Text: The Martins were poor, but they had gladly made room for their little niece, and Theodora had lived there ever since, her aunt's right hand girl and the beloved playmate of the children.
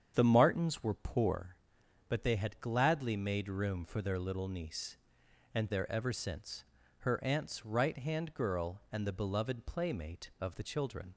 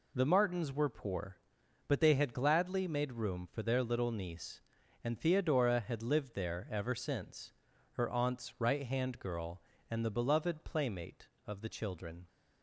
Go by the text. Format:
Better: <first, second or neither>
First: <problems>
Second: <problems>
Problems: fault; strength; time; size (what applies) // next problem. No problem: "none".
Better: second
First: starts louder than the rest; strong; until 1.1 s; 8 dB // skips "Theodora had lived"; at 5.6 s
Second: none